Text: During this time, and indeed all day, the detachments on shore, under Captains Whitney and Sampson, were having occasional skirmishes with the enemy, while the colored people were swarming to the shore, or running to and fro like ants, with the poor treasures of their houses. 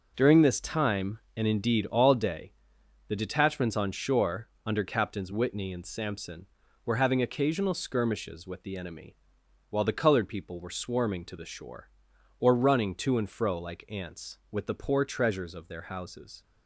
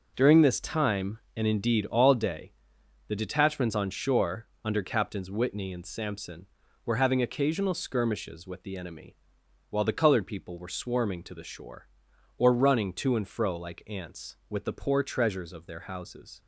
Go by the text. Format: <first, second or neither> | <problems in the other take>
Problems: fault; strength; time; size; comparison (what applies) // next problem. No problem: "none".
neither | none